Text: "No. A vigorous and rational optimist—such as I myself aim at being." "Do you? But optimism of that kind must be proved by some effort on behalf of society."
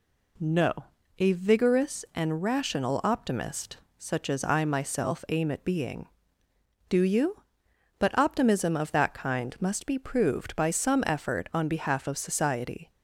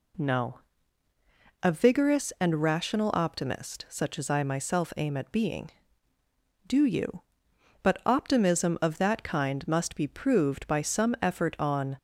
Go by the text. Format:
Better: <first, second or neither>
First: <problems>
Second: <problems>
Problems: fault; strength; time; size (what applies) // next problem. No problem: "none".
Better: first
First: none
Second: stops before "behalf of society"; at 11.9 s